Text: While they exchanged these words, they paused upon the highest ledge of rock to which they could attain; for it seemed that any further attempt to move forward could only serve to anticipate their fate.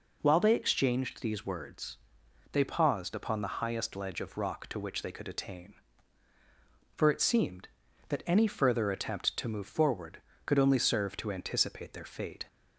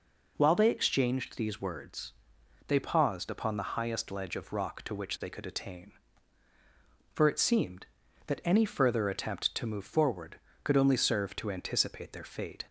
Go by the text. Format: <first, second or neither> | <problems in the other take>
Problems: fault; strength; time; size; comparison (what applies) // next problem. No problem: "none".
neither | none